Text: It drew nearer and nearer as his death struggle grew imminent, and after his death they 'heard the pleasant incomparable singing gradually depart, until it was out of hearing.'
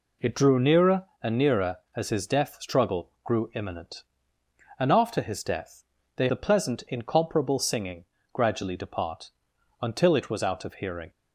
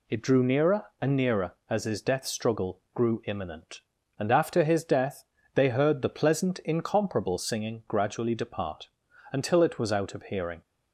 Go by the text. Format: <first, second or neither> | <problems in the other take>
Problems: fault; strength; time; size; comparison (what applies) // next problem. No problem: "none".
second | pauses between "death" and "they"; slight; at 5.8 s; 0.32 s long; slight in the second // skips "heard"; at 6.2 s // pauses between "singing" and "gradually"; slight; at 8.0 s; 0.28 s long